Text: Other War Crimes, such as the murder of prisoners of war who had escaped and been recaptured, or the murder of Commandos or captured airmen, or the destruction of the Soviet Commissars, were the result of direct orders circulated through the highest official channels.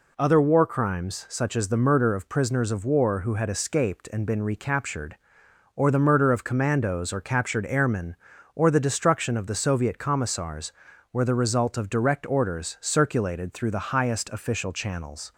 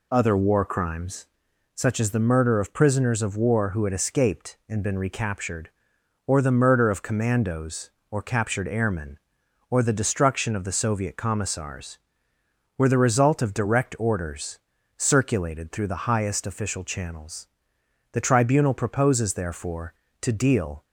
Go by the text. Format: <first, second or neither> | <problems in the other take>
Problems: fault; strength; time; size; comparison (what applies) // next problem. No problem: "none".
first | pauses between "orders" and "circulated"; at 14.5 s; 0.38 s long // goes on to say "The Tribunal proposes therefore to deal"; strong; from 18.1 s on; 2.7 s long